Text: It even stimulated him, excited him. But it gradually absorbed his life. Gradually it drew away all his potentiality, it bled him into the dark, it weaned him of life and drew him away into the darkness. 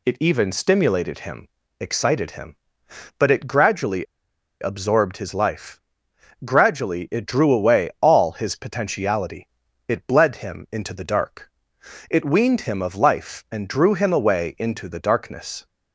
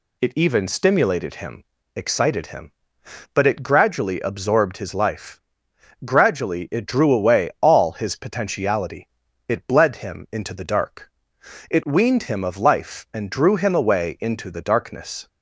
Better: second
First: pauses between "gradually" and "absorbed"; noticeable; at 4.0 s; 0.56 s long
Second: none

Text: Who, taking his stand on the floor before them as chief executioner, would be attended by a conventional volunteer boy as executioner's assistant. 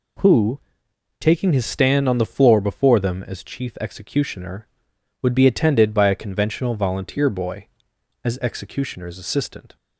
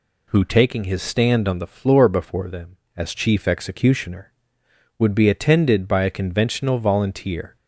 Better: first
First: none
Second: stops before "boy as executioner's assistant"; at 7.5 s

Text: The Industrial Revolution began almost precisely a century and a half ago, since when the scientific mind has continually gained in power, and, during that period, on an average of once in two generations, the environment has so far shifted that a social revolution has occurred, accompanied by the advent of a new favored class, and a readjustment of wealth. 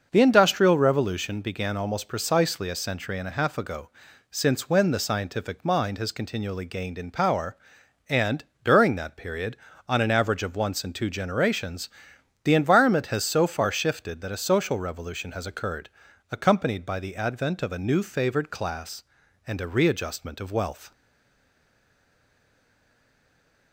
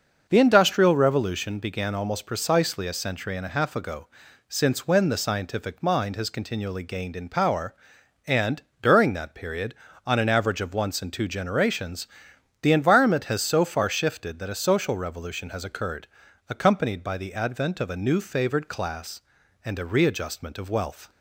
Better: second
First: starts louder than the rest; until 1.1 s; 6 dB // stays silent after the last word; strong; from 20.9 s on; 2.8 s long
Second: starts louder than the rest; until 1.3 s; 6 dB

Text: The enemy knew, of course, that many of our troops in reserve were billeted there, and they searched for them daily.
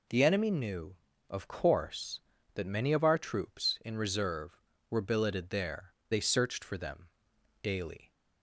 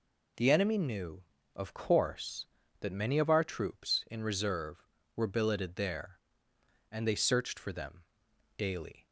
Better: second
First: skips "and"; at 6.0 s // pauses between "them" and "daily"; noticeable; at 7.0 s; 0.54 s long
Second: pauses between "them" and "daily"; noticeable; at 8.0 s; 0.54 s long

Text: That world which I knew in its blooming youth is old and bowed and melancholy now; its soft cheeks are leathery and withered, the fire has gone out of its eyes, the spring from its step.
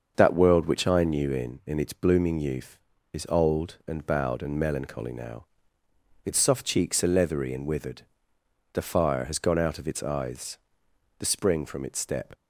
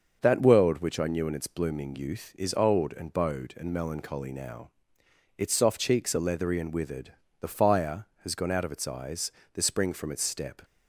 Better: second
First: starts louder than the rest; until 1.1 s; 6.5 dB // says "in" twice; at 1.6 s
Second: starts louder than the rest; until 1.2 s; 6.5 dB

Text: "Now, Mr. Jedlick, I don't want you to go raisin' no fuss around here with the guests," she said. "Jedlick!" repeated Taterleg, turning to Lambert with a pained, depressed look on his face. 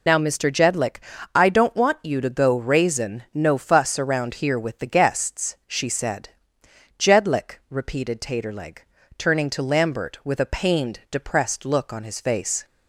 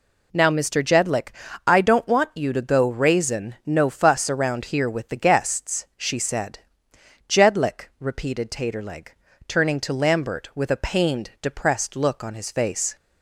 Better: second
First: loses the start of "Now"; at 0.0 s; 65 ms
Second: none

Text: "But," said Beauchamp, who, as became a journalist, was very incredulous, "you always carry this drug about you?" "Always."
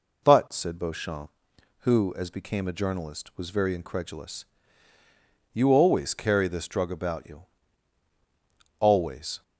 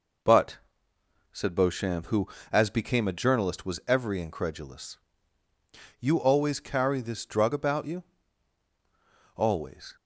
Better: first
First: none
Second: says "every" for "very"; at 3.8 s

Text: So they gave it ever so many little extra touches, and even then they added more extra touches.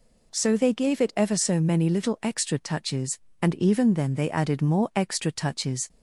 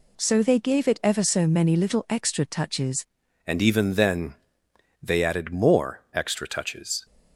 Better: first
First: none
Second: changes voice at "and"; from 3.4 s on; 3.6 s long // pauses between "then" and "they"; noticeable; at 4.3 s; 0.70 s long

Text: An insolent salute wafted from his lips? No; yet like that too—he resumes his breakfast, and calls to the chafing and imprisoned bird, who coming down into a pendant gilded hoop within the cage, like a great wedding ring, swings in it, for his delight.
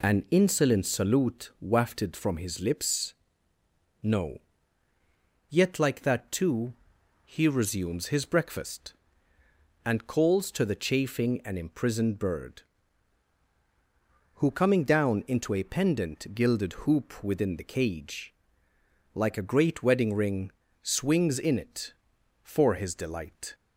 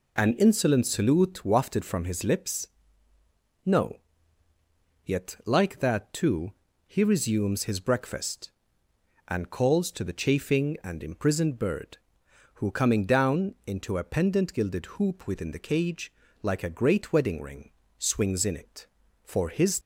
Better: first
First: none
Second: stops before "delight"; at 19.8 s

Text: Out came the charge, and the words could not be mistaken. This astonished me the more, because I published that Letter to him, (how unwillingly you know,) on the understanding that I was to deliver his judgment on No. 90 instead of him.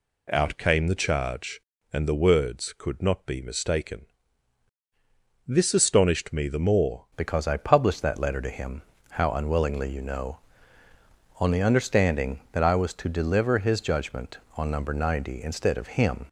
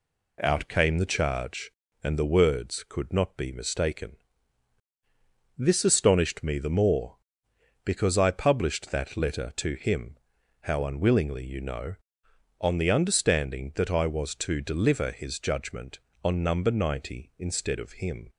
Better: second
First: changes voice at "because"; from 7.1 s on; 9.1 s long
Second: none

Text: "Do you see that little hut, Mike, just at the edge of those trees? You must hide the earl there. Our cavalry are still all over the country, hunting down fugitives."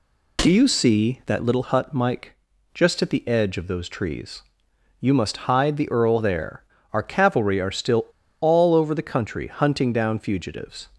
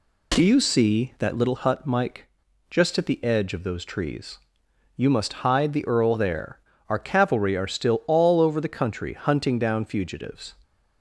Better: second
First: pauses between "still" and "all"; slight; at 8.0 s; 0.35 s long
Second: none

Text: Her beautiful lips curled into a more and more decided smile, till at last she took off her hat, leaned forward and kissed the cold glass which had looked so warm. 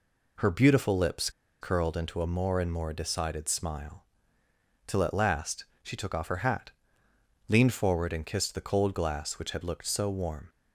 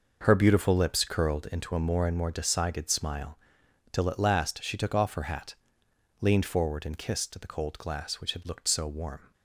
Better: second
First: pauses between "lips" and "curled"; slight; at 1.2 s; 0.31 s long // pauses between "last" and "she"; slight; at 5.6 s; 0.18 s long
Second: none

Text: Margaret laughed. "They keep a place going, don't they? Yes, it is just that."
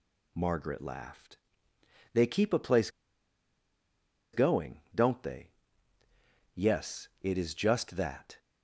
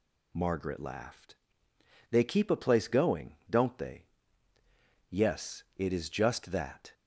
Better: second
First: pauses between "place" and "going"; strong; at 2.8 s; 1.4 s long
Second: none

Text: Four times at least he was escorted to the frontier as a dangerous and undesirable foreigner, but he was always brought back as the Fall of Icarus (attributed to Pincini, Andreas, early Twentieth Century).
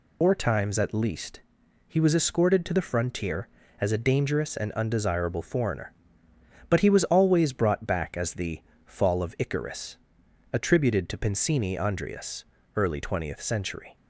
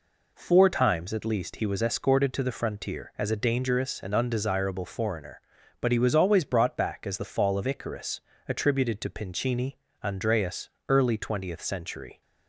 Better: second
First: loses the start of "Four"; at 0.2 s; 115 ms // pauses between "least" and "he"; noticeable; at 1.4 s; 0.46 s long // pauses between "the" and "Fall"; slight; at 8.6 s; 0.24 s long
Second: none

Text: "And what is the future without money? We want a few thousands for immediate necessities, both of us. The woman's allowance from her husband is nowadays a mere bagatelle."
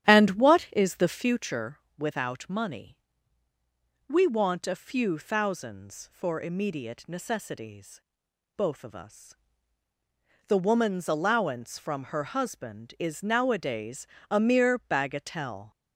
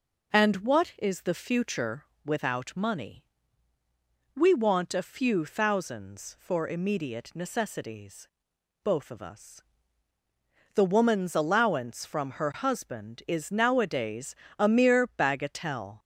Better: second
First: starts louder than the rest; strong; until 1.4 s; 11 dB // pauses between "future" and "without"; slight; at 1.7 s; 0.17 s long // pauses between "nowadays" and "a"; slight; at 14.0 s; 0.24 s long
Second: pauses between "future" and "without"; slight; at 2.0 s; 0.18 s long // pauses between "nowadays" and "a"; slight; at 14.3 s; 0.24 s long

